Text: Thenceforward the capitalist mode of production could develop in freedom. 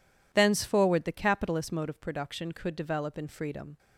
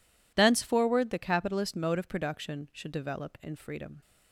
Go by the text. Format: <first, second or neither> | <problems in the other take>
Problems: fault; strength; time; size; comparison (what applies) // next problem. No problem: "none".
first | says "should" for "could"; at 2.7 s